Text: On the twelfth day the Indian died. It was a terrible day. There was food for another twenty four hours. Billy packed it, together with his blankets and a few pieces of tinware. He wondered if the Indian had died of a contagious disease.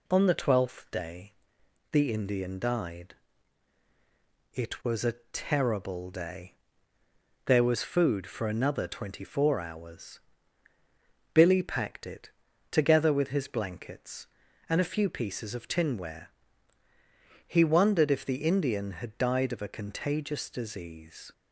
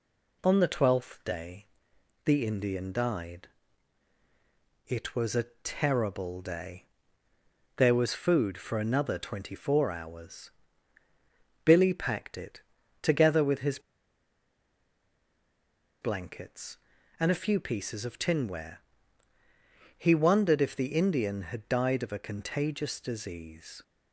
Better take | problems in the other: first | pauses between "day" and "the"; noticeable; at 1.6 s; 0.58 s long; noticeable in the first // pauses between "a" and "terrible"; slight; at 5.4 s; 0.18 s long; slight in the first // pauses between "his" and "blankets"; strong; at 13.7 s; 2.2 s long

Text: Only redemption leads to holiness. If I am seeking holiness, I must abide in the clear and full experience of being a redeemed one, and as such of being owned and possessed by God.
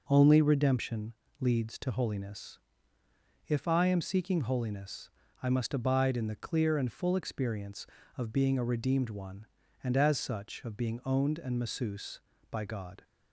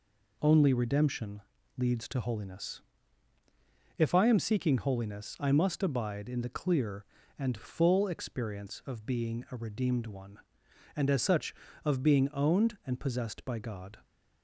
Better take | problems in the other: second | pauses between "redemption" and "leads"; slight; at 1.1 s; 0.28 s long; slight in the second // says "masseuse" for "possessed"; at 11.5 s

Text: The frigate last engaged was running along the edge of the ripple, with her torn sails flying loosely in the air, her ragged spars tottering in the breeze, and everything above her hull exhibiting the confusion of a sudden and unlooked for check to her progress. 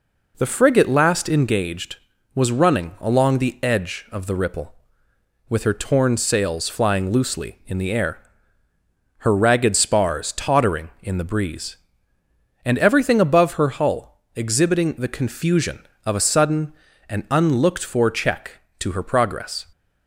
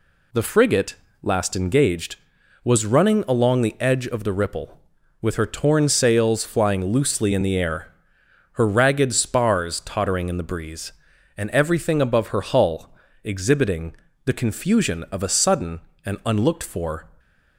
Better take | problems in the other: first | pauses between "frigate" and "last"; slight; at 0.9 s; 0.26 s long // pauses between "hull" and "exhibiting"; slight; at 12.9 s; 0.28 s long // pauses between "exhibiting" and "the"; slight; at 13.9 s; 0.30 s long // stops before "check to her progress"; at 17.1 s

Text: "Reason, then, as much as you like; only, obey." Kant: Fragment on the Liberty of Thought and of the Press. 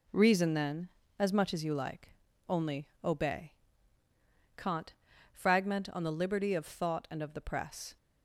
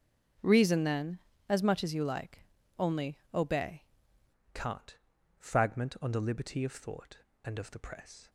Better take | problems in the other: first | starts louder than the rest; until 1.7 s; 7 dB // changes voice at "Kant"; from 4.5 s on; 3.7 s long

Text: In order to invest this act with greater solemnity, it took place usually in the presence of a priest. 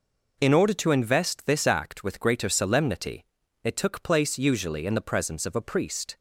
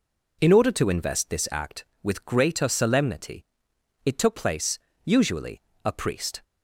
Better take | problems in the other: first | pauses between "place" and "usually"; slight; at 4.7 s; 0.26 s long // skips "in the presence of"; at 5.7 s

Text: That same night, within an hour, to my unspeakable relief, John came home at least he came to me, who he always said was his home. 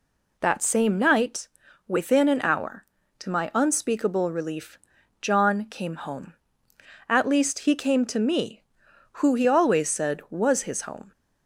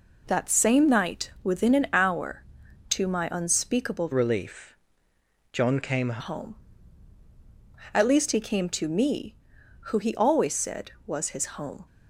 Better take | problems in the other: first | changes voice from "relief" to "came"; from 4.1 to 6.2 s; 2.1 s long

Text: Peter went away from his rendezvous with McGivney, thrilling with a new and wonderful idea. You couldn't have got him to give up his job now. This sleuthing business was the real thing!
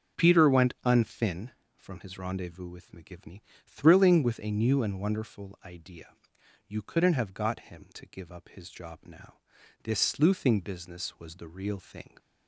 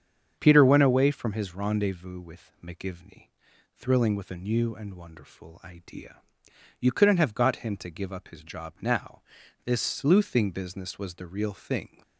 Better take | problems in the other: second | starts louder than the rest; until 1.2 s; 6.5 dB; strong in the second // says "unfin" for "away"; at 0.8 s

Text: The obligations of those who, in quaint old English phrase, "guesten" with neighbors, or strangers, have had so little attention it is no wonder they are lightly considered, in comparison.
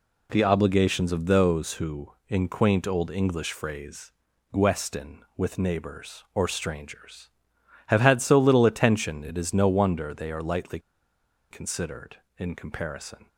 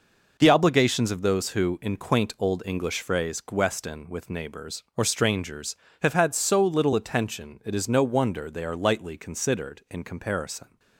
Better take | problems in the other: second | pauses between "lightly" and "considered"; noticeable; at 10.7 s; 0.71 s long

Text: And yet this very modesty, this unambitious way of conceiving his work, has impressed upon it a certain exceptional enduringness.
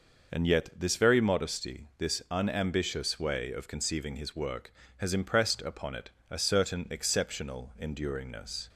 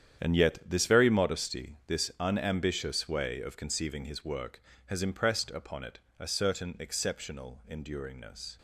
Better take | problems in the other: first | gets quieter; strong; throughout; 13.5 dB // pauses between "it" and "a"; slight; at 5.9 s; 0.18 s long; slight in the first

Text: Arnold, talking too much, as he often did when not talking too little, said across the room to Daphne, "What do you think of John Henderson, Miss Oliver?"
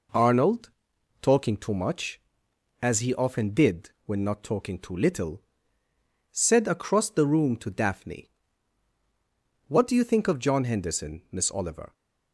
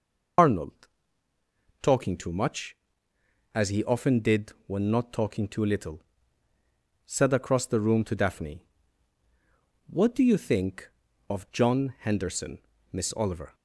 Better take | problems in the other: first | loses the start of "Arnold"; at 0.3 s; 70 ms // pauses between "did" and "when"; slight; at 4.5 s; 0.16 s long

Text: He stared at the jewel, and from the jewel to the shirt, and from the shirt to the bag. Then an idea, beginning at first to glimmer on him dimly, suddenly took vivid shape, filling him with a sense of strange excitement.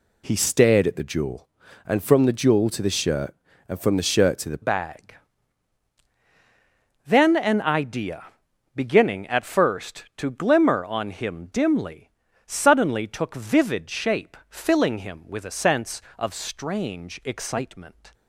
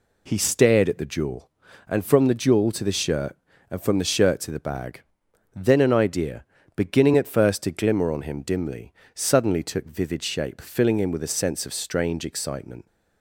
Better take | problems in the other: second | changes voice at "bag"; from 4.6 s on; 13.5 s long

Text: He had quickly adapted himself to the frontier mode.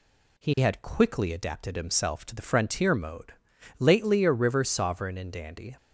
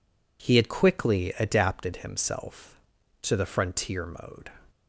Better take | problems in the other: second | goes on to say "Lately a river sovereign and dandy"; strong; from 3.7 s on; 1.9 s long

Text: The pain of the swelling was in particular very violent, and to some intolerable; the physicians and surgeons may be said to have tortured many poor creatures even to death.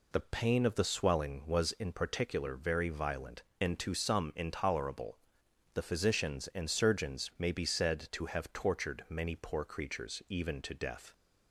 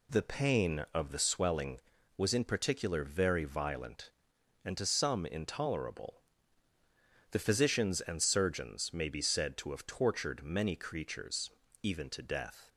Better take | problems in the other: first | skips "poor"; at 10.7 s // pauses between "creatures" and "even"; slight; at 11.5 s; 0.34 s long

